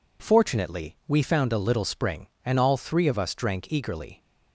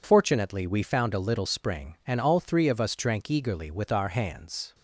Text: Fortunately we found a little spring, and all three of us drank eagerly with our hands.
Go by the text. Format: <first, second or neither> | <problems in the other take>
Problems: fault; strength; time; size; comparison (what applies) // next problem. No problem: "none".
second | stops before "with our hands"; at 4.1 s